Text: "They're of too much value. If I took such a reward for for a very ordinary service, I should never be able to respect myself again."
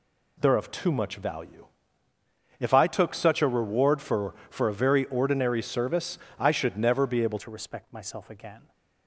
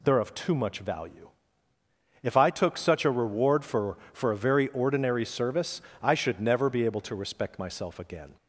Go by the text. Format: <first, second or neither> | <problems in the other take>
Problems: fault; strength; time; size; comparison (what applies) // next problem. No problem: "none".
second | changes voice at "to"; from 7.3 s on; 1.4 s long